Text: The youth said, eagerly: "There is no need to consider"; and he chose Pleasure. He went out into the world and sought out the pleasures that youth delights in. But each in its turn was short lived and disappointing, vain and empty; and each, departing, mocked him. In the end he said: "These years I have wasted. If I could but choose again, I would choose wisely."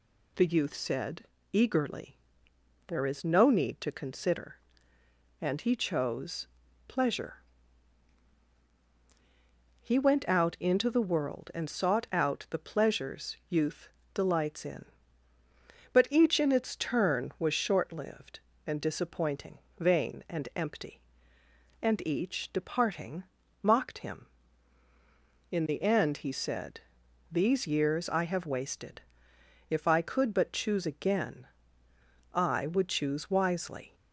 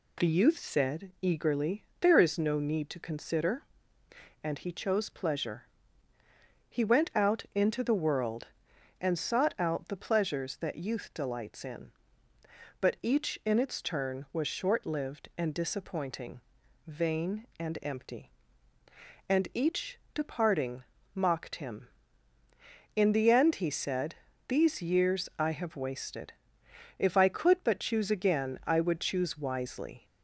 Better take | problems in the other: second | pauses between "chose" and "Pleasure"; at 6.4 s; 0.40 s long // skips "that"; at 13.4 s // pauses between "youth" and "delights"; slight; at 13.8 s; 0.24 s long

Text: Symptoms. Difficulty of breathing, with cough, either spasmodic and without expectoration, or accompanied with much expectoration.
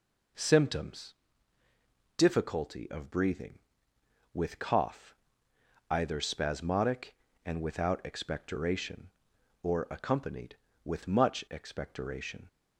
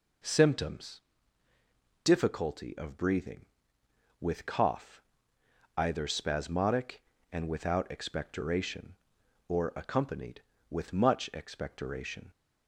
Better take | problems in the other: neither | none

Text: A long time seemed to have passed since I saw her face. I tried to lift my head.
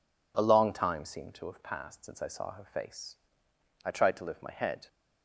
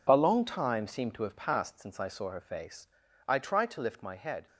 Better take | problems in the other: first | gets quieter; strong; throughout; 10.5 dB

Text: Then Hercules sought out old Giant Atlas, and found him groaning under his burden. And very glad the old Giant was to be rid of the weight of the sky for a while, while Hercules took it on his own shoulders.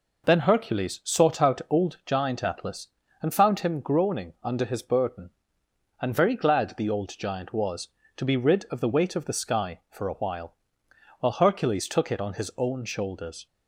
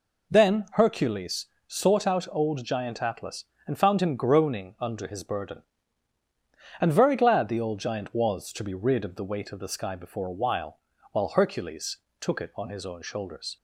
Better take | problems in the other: first | pauses between "Hercules" and "sought"; slight; at 1.4 s; 0.20 s long // says "before" for "for"; at 9.9 s // pauses between "Hercules" and "took"; slight; at 11.9 s; 0.22 s long

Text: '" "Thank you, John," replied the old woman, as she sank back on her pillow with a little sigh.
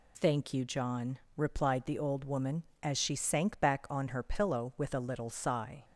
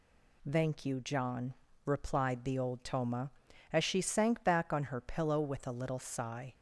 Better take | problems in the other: first | says "toma" for "woman"; at 2.8 s

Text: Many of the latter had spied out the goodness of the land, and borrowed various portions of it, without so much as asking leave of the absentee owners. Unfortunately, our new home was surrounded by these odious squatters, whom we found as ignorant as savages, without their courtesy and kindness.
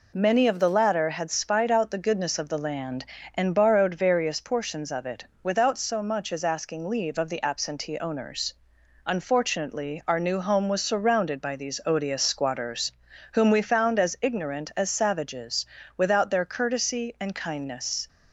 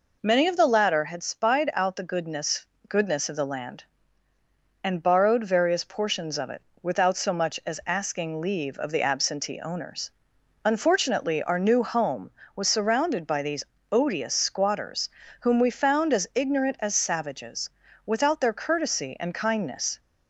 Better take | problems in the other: first | says "goodness" twice; at 2.8 s // pauses between "these" and "odious"; slight; at 13.6 s; 0.30 s long

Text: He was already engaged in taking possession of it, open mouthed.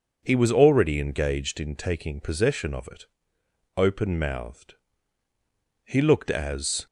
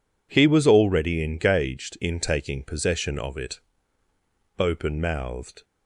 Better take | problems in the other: second | goes on to say "He looked as"; noticeable; from 5.8 s on; 1.0 s long

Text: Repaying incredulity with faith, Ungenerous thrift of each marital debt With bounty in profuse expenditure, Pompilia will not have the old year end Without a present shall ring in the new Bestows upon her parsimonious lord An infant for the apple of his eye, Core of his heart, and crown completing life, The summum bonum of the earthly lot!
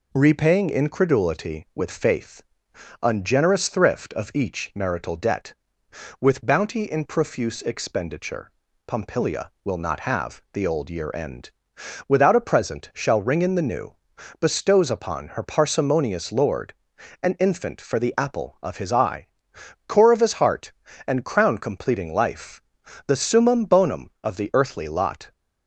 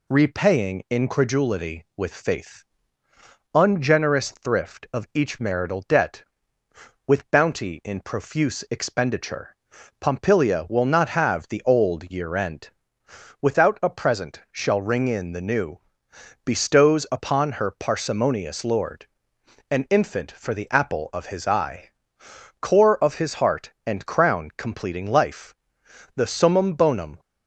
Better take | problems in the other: first | pauses between "end" and "Without"; noticeable; at 12.6 s; 0.72 s long; noticeable in the first // pauses between "new" and "Bestows"; noticeable; at 15.7 s; 0.68 s long; noticeable in the first // pauses between "lord" and "An"; noticeable; at 19.0 s; 0.62 s long; noticeable in the first // stops before "of the earthly lot"; at 27.1 s

